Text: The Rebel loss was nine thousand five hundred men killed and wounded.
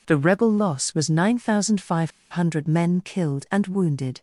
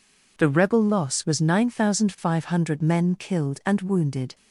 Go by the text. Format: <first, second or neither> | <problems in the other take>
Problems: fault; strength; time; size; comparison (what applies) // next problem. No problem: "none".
second | pauses between "five" and "hundred"; slight; at 2.1 s; 0.19 s long